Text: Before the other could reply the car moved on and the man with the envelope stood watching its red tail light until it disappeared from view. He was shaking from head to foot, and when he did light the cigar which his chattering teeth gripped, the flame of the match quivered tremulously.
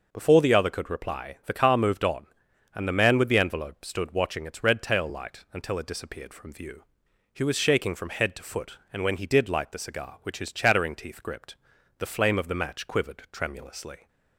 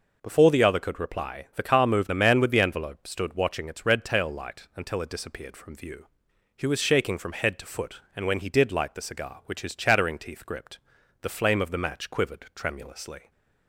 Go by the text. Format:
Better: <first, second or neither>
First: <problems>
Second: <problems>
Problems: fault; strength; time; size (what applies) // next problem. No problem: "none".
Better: first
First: none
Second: skips "on and"; at 2.0 s